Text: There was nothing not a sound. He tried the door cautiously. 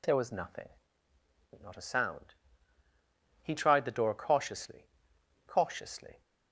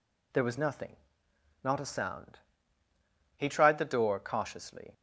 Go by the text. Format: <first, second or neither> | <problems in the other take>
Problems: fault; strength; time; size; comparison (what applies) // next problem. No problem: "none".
second | pauses between "nothing" and "not"; noticeable; at 0.6 s; 0.94 s long; noticeable in the second // says "cautiously" twice; at 5.4 s